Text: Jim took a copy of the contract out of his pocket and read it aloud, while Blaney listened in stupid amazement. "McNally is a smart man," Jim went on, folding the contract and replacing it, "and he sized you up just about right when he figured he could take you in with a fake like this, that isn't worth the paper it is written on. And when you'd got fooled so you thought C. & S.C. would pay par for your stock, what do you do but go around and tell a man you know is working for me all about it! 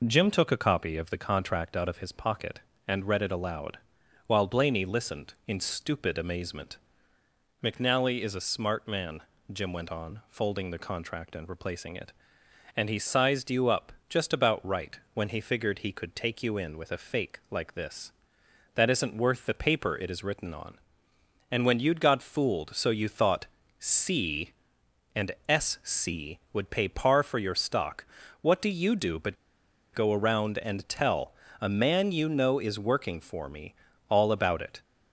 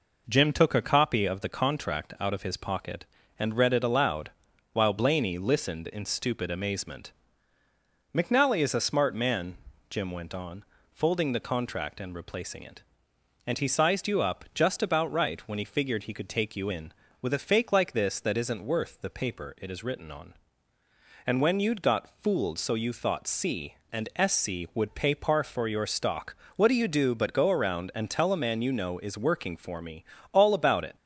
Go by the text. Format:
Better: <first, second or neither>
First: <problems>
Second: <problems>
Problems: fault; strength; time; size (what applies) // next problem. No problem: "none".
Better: second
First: pauses between "up" and "just"; slight; at 13.9 s; 0.16 s long // pauses between "thought" and "C"; slight; at 23.4 s; 0.34 s long // pauses between "but" and "go"; noticeable; at 29.3 s; 0.57 s long // pauses between "tell" and "a"; slight; at 31.3 s; 0.30 s long // pauses between "me" and "all"; slight; at 33.7 s; 0.32 s long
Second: pauses between "me" and "all"; slight; at 30.0 s; 0.28 s long